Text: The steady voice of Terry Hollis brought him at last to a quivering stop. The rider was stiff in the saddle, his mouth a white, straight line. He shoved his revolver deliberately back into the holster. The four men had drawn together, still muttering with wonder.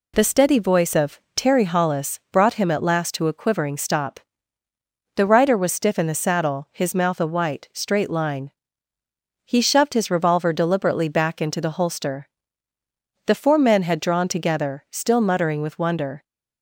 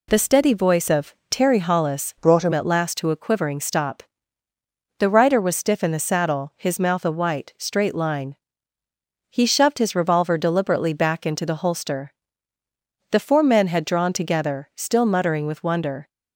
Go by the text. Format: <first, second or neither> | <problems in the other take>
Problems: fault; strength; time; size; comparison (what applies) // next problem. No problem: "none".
first | pauses between "of" and "Terry"; slight; at 1.1 s; 0.16 s long; slight in the first // changes voice from "brought" to "him"; from 2.1 to 2.5 s; 0.4 s long